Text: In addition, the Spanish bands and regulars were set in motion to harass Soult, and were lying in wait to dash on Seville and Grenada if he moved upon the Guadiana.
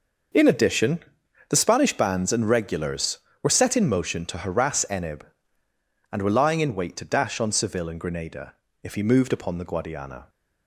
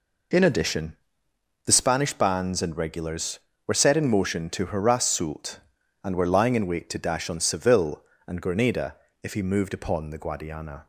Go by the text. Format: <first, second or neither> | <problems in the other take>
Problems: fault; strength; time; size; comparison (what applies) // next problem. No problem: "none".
second | starts louder than the rest; until 1.8 s; 6 dB // says "Enib" for "Soult"; at 4.8 s // pauses between "Grenada" and "if"; slight; at 8.5 s; 0.28 s long; slight in the second